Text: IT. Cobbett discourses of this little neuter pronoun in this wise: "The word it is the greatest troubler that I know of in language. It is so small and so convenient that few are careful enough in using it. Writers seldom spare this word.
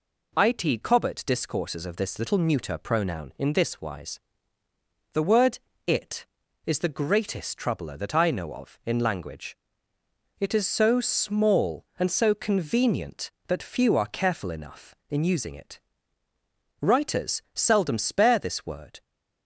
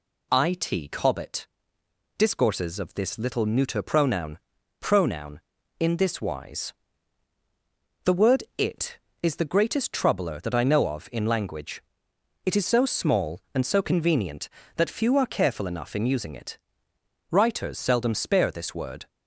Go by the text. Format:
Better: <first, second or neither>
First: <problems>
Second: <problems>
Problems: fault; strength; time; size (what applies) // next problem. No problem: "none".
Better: first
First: pauses between "word" and "it"; slight; at 5.5 s; 0.26 s long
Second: pauses between "Cobbett" and "discourses"; noticeable; at 1.4 s; 0.72 s long // says "pronoun" twice; at 4.7 s // pauses between "word" and "it"; slight; at 8.4 s; 0.16 s long